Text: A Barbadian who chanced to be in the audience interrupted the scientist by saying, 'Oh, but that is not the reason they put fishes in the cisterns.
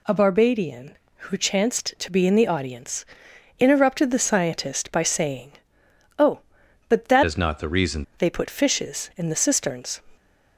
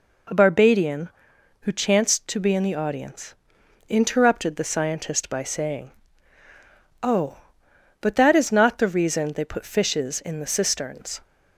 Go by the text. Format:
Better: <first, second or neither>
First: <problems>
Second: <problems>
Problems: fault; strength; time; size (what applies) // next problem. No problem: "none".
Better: second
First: pauses between "audience" and "interrupted"; noticeable; at 3.0 s; 0.52 s long // changes voice from "is" to "reason"; from 7.2 to 8.0 s; 0.8 s long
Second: pauses between "audience" and "interrupted"; noticeable; at 3.3 s; 0.52 s long